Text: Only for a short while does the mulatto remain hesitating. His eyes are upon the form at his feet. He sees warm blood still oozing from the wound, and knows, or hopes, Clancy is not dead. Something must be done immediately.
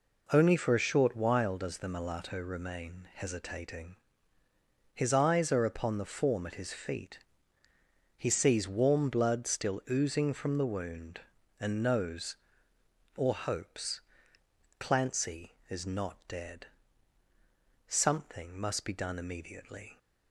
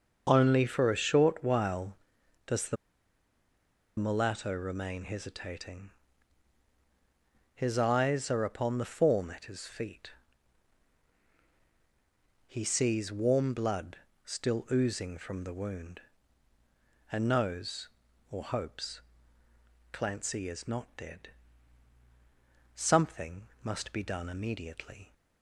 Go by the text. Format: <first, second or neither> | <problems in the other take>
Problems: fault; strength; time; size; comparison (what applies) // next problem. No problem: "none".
first | starts louder than the rest; until 1.3 s; 6.5 dB // pauses between "the" and "mulatto"; at 2.7 s; 1.2 s long // pauses between "blood" and "still"; slight; at 13.9 s; 0.28 s long // pauses between "Something" and "must"; slight; at 23.4 s; 0.16 s long